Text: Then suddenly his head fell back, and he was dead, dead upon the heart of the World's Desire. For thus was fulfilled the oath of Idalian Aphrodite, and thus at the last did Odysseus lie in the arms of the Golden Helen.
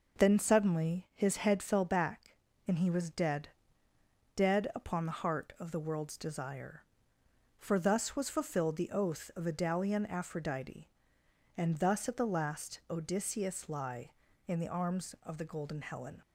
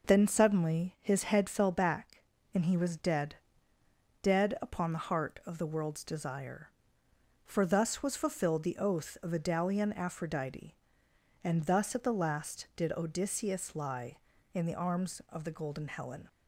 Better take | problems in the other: second | skips "did"; at 12.8 s

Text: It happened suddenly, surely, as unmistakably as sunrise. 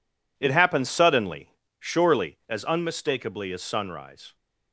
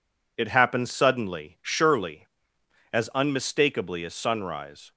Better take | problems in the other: neither | none

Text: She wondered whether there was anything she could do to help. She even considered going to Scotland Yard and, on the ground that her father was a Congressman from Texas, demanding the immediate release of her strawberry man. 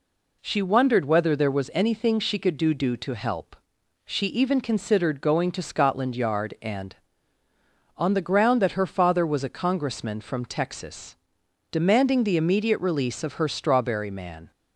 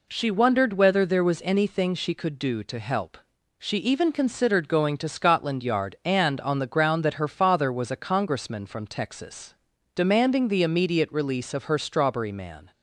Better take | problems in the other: second | says "do" twice; at 2.7 s

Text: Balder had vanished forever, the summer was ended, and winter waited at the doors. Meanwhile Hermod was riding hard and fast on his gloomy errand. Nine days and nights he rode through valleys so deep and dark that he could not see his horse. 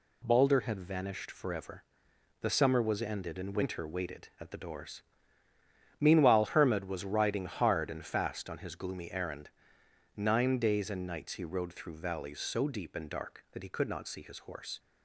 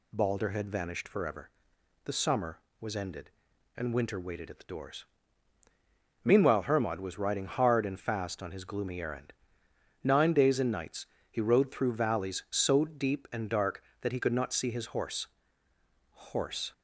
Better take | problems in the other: first | pauses between "nights" and "he"; slight; at 11.0 s; 0.24 s long // says "horse" twice; at 16.3 s

